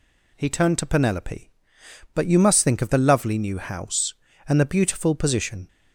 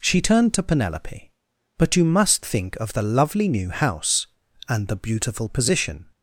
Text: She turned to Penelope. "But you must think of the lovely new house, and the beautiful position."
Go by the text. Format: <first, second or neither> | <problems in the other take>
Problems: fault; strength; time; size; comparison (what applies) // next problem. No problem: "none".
second | says "He" for "She"; at 0.3 s